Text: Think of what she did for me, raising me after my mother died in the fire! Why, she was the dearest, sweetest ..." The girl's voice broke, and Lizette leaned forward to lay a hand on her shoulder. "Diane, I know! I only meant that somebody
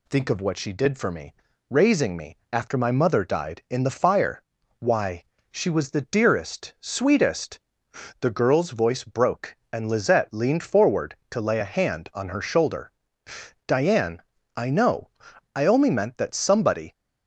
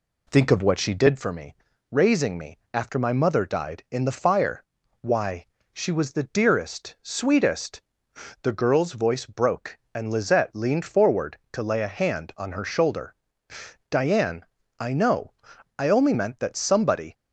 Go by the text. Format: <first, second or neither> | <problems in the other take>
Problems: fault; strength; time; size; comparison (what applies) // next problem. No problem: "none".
first | starts louder than the rest; slight; until 1.2 s; 2.5 dB // pauses between "me" and "after"; slight; at 2.5 s; 0.16 s long; slight in the first